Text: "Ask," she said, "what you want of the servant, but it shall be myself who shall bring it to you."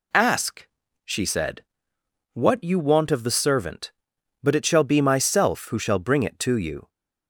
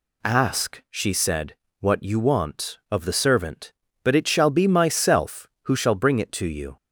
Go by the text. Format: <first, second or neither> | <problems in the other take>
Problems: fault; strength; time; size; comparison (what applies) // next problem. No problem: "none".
neither | none